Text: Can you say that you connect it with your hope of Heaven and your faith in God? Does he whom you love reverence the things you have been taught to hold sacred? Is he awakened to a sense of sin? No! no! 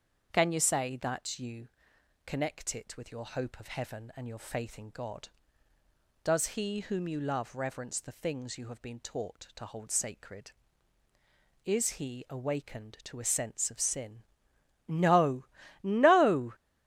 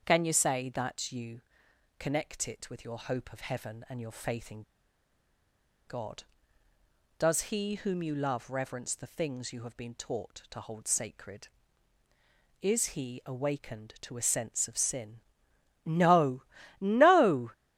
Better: first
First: starts louder than the rest; until 1.3 s; 7 dB // pauses between "you" and "connect"; noticeable; at 1.6 s; 0.58 s long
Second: starts louder than the rest; until 1.1 s; 7 dB // pauses between "you" and "connect"; noticeable; at 1.4 s; 0.58 s long // pauses between "in" and "God"; at 4.6 s; 1.2 s long

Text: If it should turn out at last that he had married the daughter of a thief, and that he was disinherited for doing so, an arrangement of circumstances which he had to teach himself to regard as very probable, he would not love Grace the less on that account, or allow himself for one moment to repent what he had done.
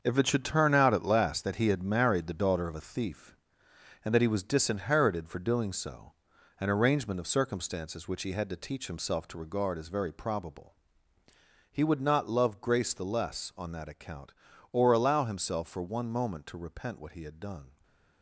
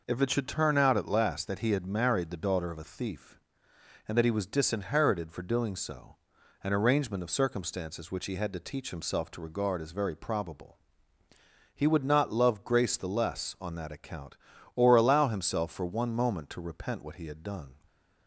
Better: second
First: gets quieter; strong; throughout; 9 dB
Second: none

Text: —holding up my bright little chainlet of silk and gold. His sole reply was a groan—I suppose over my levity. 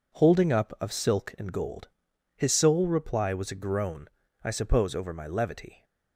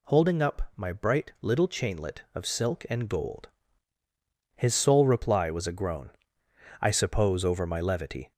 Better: second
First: skips "my bright little chainlet"; at 0.7 s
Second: none

